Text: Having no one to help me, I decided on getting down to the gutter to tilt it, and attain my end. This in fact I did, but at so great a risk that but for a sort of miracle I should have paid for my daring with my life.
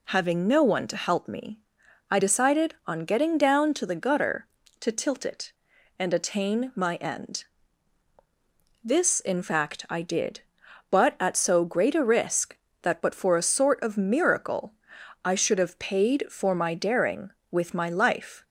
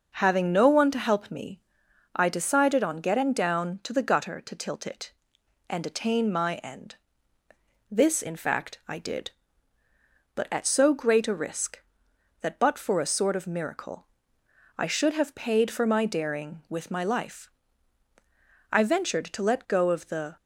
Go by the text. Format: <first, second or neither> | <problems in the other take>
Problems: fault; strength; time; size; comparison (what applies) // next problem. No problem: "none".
first | pauses between "miracle" and "I"; noticeable; at 14.0 s; 0.72 s long; noticeable in the first // goes on to say "I ventured to let go of the"; from 18.7 s on; 1.6 s long